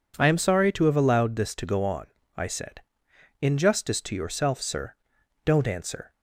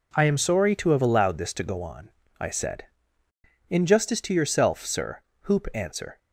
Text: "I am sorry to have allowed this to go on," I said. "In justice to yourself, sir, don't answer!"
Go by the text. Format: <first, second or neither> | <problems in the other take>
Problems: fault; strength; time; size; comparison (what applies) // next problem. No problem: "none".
first | says "hoop" for "don't"; at 5.4 s